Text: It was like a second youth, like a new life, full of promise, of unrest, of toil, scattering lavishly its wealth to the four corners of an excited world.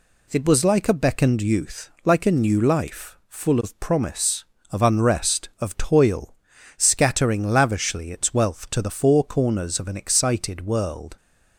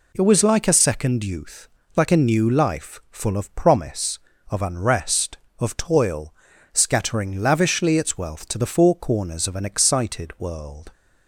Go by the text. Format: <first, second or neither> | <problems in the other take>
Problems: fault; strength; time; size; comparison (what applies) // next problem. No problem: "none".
second | says "beckoned" for "second"; at 0.9 s